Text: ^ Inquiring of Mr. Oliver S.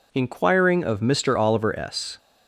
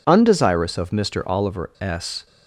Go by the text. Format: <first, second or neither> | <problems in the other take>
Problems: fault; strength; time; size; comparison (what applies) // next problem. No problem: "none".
first | says "Undesirous" for "Inquiring"; at 0.0 s